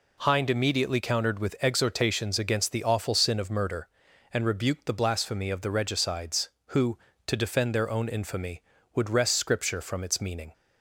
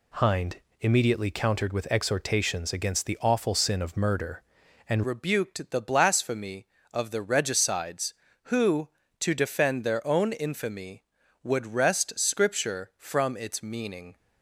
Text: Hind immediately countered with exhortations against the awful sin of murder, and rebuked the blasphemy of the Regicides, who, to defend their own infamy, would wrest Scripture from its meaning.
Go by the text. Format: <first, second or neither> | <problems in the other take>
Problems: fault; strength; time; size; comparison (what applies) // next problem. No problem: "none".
first | pauses between "Hind" and "immediately"; slight; at 0.5 s; 0.24 s long // changes voice at "rebuked"; from 5.0 s on; 9.1 s long